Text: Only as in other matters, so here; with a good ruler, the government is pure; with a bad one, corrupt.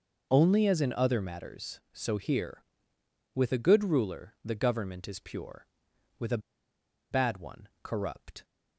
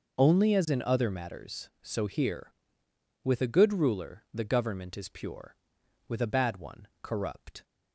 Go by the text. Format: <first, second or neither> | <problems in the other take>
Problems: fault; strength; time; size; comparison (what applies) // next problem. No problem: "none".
second | pauses between "a" and "bad"; noticeable; at 6.3 s; 0.72 s long